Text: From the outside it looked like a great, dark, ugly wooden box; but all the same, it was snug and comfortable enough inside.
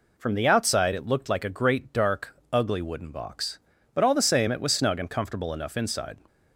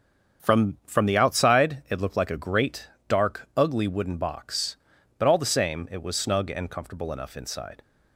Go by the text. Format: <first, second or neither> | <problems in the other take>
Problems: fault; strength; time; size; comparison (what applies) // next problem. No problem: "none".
first | starts louder than the rest; until 1.4 s; 6.5 dB // says "From" twice; at 0.8 s